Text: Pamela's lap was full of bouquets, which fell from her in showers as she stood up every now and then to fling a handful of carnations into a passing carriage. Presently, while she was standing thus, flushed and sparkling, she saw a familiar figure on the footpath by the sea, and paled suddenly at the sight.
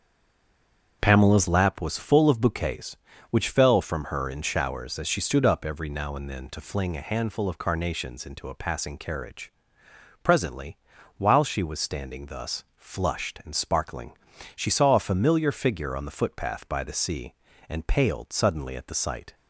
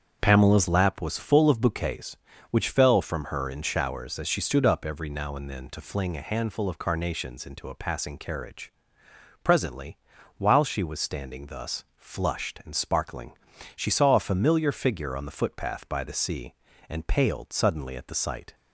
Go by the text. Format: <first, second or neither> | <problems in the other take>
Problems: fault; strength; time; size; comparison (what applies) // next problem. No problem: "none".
second | stays silent before the first word; until 1.0 s; 1.0 s long // starts louder than the rest; strong; until 2.0 s; 7.5 dB; strong in the second